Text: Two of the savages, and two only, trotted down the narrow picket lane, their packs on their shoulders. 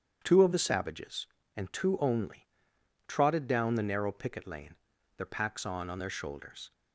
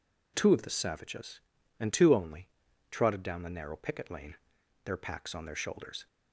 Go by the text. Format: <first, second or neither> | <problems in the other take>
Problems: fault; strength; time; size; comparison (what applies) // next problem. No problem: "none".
second | starts louder than the rest; strong; until 1.2 s; 8.5 dB // says "on" twice; at 5.8 s